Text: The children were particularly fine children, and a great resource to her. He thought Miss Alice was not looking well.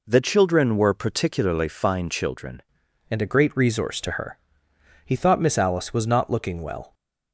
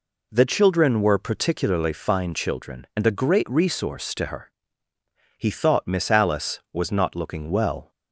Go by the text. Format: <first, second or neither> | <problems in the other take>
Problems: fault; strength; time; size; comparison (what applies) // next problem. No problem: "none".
second | changes voice at "and"; from 3.0 s on; 3.9 s long